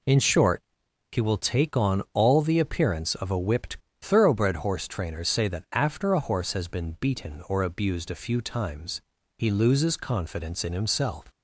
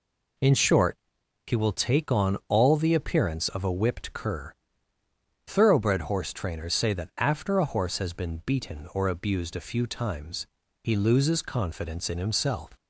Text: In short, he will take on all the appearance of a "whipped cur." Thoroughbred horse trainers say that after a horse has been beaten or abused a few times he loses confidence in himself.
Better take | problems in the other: second | skips "cur"; at 3.8 s // pauses between "times" and "he"; at 8.9 s; 0.38 s long; also in the second

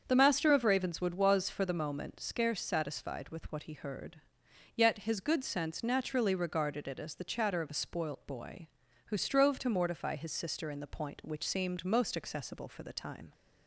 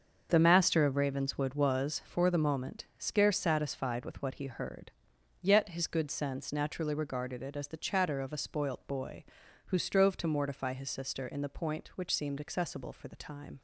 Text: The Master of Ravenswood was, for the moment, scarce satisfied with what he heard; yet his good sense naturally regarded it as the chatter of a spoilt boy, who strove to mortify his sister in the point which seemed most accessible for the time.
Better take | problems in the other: first | starts louder than the rest; until 1.3 s; 6.5 dB; also in the first // skips "most"; at 12.4 s

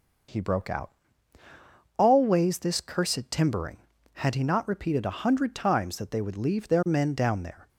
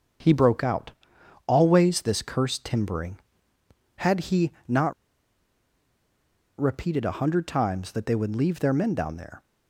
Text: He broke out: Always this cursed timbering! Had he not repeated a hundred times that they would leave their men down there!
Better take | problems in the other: first | starts louder than the rest; until 1.7 s; 6.5 dB // pauses between "he" and "not"; slight; at 4.5 s; 0.16 s long // pauses between "not" and "repeated"; strong; at 4.9 s; 1.6 s long

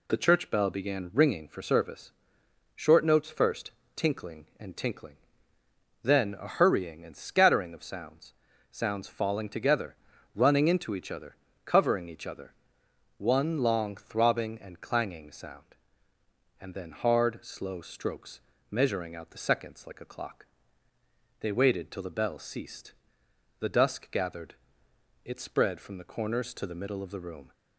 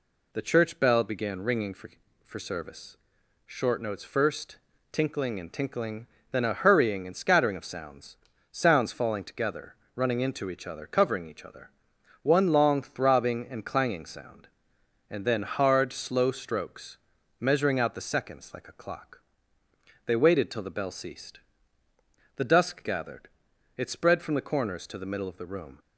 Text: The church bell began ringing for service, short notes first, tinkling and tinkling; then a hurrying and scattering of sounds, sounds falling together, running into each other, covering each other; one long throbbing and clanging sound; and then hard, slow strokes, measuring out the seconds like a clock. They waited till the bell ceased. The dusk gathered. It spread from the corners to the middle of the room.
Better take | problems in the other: first | says "for" twice; at 2.2 s

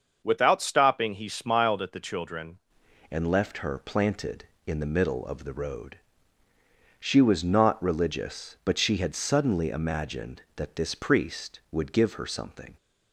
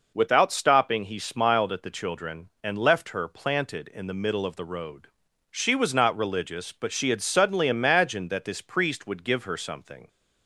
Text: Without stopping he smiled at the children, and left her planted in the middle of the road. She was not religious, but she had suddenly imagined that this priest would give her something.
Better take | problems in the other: second | starts louder than the rest; until 1.2 s; 6.5 dB // changes voice at "and"; from 3.1 s on; 9.6 s long

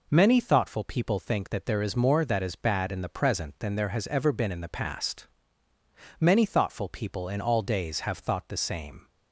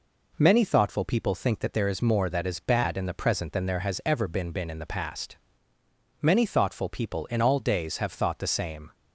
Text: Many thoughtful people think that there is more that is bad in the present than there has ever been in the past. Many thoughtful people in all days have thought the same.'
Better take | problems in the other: first | says "been" twice; at 4.4 s

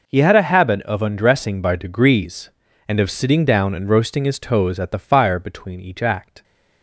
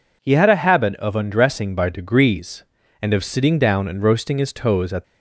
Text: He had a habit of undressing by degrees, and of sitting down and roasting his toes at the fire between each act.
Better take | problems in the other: first | stops before "the fire between each act"; at 5.0 s

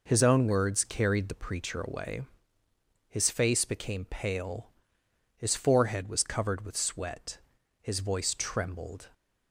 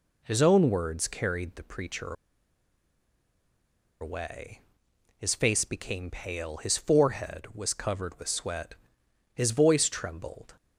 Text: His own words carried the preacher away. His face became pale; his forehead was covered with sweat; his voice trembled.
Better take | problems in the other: first | pauses between "preacher" and "away"; strong; at 2.1 s; 1.8 s long

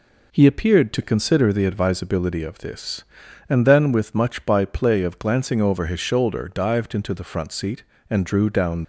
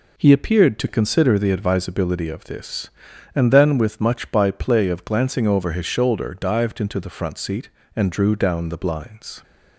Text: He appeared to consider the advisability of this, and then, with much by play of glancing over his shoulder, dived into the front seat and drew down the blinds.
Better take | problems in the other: second | stops before "the blinds"; at 8.8 s

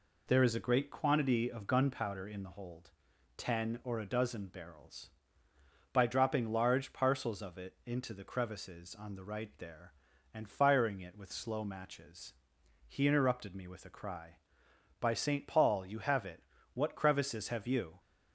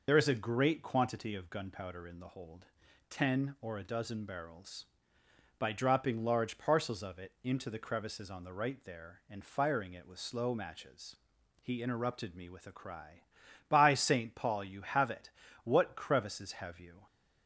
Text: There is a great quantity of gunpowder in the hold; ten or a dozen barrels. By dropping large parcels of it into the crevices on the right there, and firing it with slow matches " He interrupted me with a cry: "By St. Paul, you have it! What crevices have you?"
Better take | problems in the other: first | loses the start of "There"; at 0.0 s; 55 ms

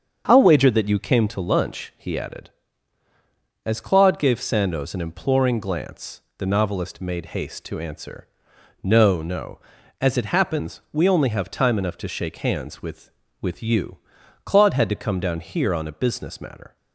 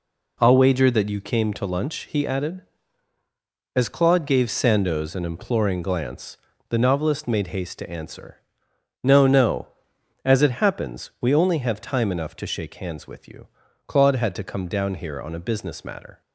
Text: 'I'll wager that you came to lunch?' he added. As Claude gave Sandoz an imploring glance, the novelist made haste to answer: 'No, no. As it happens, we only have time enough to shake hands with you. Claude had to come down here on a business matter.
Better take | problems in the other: second | starts louder than the rest; until 1.2 s; 7 dB // says "with" twice; at 13.4 s

